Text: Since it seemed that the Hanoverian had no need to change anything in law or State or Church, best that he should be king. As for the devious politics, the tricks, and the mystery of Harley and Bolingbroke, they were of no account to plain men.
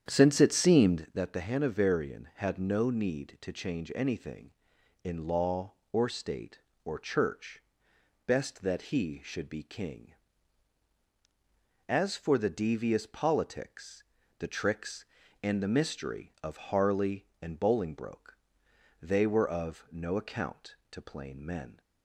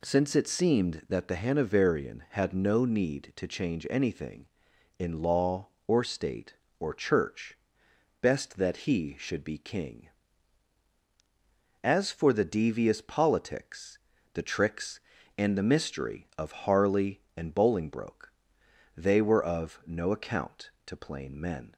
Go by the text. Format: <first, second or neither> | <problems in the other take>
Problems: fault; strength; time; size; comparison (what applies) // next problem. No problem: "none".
second | starts louder than the rest; strong; until 1.1 s; 9 dB